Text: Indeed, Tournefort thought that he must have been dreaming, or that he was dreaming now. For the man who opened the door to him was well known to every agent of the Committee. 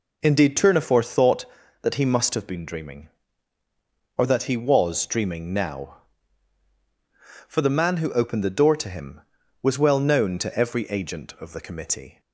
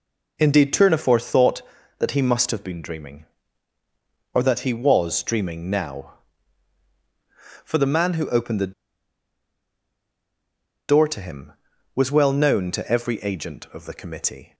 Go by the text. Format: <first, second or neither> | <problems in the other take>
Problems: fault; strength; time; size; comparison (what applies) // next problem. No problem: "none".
first | pauses between "the" and "door"; strong; at 8.7 s; 2.1 s long